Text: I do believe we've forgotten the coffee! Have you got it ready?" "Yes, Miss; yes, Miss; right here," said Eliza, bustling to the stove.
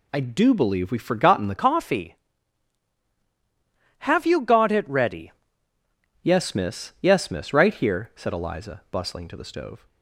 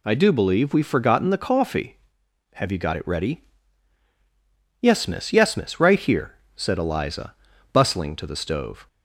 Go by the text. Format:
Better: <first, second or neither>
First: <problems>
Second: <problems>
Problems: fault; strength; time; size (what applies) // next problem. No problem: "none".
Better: second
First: changes voice from "coffee" to "ready"; from 1.5 to 5.3 s; 3.8 s long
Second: none